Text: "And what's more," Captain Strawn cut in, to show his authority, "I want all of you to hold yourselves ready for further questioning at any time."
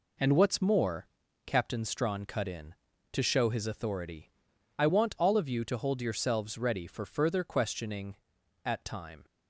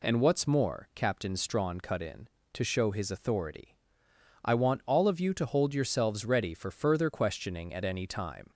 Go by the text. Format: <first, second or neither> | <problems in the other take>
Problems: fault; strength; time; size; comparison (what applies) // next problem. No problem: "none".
second | skips "any"; at 8.8 s